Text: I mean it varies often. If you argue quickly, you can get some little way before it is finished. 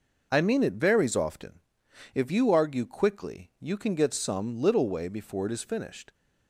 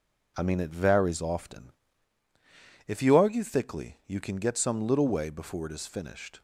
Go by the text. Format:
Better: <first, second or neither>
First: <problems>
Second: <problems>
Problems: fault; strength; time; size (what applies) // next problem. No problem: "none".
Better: first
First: none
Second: says "thickly" for "quickly"; at 3.4 s